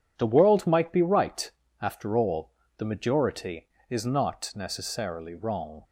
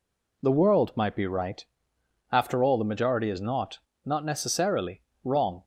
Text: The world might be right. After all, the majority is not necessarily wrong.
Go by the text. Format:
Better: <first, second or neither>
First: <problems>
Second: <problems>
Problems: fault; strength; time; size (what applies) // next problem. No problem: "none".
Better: first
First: none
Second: says "not" twice; at 4.0 s // pauses between "necessarily" and "wrong"; slight; at 5.0 s; 0.22 s long